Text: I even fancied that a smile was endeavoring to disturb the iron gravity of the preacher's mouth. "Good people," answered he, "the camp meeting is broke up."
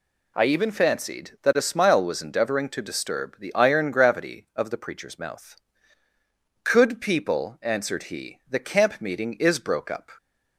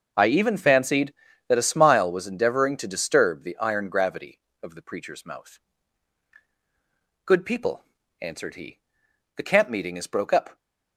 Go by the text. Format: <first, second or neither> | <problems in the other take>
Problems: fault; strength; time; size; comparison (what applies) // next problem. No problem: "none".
second | says "Could" for "Good"; at 6.6 s